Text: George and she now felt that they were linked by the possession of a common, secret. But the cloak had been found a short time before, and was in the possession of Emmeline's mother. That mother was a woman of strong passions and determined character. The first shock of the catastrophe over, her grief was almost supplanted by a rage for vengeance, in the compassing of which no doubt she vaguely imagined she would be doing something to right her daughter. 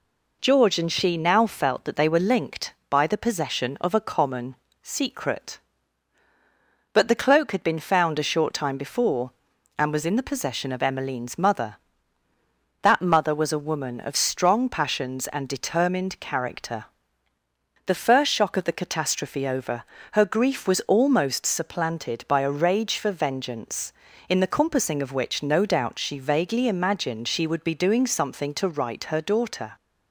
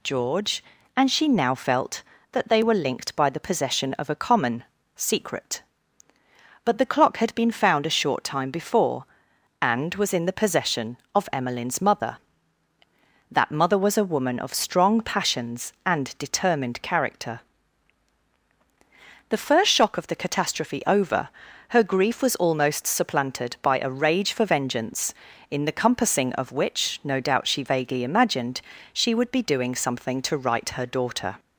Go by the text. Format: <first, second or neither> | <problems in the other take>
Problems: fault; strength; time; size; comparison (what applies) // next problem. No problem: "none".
first | says "clock" for "cloak"; at 6.8 s // pauses between "imagined" and "she"; slight; at 28.6 s; 0.32 s long